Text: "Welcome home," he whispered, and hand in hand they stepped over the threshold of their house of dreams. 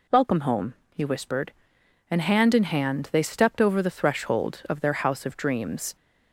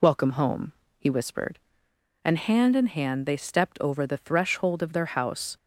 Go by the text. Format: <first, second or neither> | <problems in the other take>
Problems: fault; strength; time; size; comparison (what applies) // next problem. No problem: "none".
first | stops before "of dreams"; at 5.5 s